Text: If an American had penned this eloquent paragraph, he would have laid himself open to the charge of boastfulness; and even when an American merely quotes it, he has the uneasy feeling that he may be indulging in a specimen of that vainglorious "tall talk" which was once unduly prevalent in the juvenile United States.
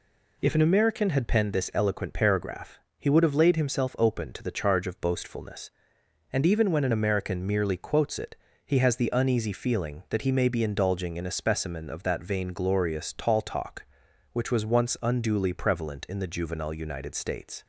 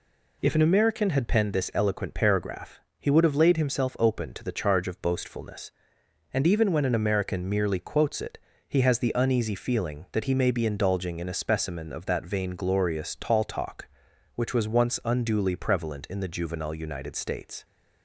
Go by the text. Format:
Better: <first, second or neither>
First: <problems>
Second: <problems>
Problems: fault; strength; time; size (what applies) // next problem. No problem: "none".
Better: neither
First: none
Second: none